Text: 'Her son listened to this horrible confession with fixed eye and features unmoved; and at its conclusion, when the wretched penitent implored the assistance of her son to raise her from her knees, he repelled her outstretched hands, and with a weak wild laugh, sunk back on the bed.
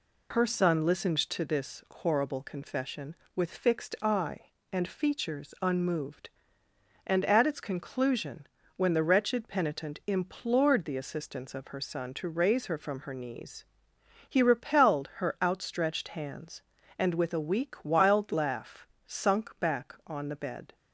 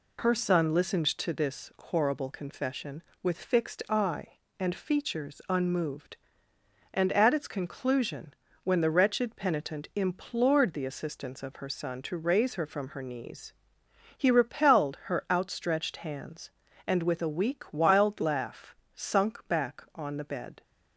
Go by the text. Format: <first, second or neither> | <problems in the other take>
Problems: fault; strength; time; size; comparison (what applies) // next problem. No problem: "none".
neither | none